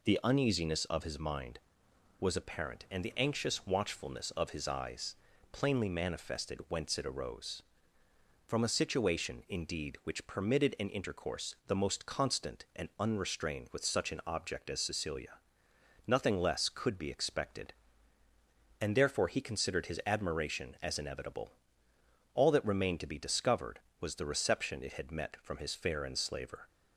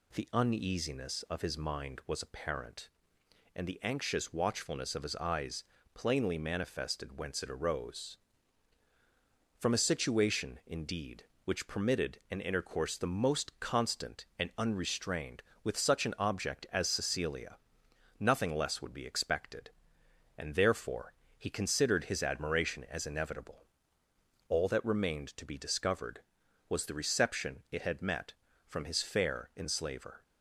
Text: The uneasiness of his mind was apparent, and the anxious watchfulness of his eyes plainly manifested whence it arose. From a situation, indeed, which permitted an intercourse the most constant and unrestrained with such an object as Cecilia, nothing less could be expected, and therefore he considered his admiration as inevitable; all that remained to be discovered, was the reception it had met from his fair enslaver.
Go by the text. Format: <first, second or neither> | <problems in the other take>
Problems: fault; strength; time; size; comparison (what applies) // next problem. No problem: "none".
first | pauses between "eyes" and "plainly"; slight; at 5.6 s; 0.30 s long; slight in the first // says "would" for "could"; at 18.8 s // pauses between "therefore" and "he"; slight; at 21.1 s; 0.24 s long